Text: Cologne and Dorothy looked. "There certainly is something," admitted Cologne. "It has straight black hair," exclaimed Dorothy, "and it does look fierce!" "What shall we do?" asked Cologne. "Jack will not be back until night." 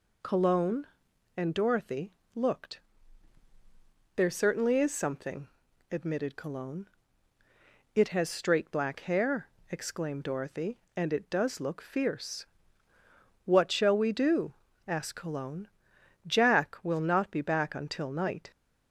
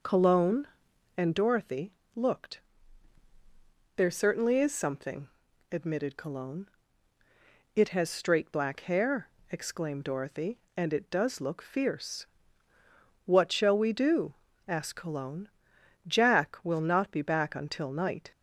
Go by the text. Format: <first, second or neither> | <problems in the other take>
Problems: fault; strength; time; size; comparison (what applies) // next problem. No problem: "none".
first | starts louder than the rest; noticeable; until 1.6 s; 5.5 dB // pauses between "Dorothy" and "looked"; slight; at 1.9 s; 0.24 s long; slight in the first